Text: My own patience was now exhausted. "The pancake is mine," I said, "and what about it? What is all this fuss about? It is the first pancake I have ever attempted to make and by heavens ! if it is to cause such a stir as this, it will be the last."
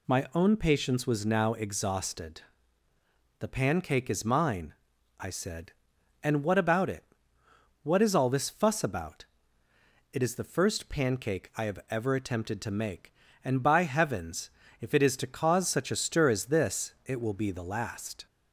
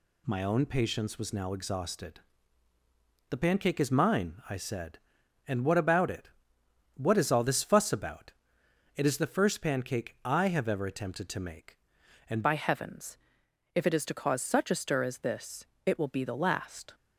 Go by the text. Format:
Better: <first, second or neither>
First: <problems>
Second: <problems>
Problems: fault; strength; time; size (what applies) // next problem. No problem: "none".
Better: first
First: none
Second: changes voice at "by"; from 12.4 s on; 4.5 s long